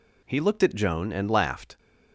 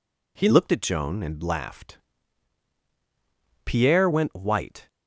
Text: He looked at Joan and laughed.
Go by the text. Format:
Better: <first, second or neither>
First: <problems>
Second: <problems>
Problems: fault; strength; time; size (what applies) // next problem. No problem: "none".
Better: first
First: none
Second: goes on to say "Pierre went white"; noticeable; from 3.6 s on; 1.2 s long